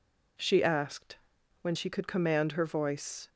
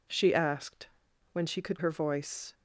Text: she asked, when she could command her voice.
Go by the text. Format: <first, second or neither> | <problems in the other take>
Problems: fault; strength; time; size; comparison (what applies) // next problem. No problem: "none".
first | skips "command"; at 1.7 s